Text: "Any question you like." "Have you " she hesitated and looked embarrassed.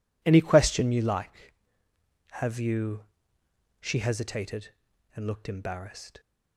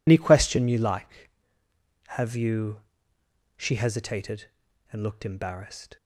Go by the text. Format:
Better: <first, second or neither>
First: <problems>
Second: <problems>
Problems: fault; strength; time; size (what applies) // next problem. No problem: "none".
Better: first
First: none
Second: loses the start of "Any"; at 0.0 s; 65 ms